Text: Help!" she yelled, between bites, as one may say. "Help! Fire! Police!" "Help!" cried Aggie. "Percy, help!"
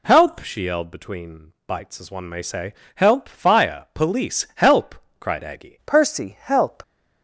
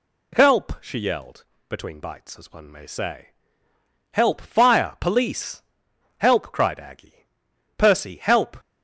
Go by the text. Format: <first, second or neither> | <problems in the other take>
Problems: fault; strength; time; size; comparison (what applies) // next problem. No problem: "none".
second | changes voice at "Percy"; from 5.8 s on; 1.0 s long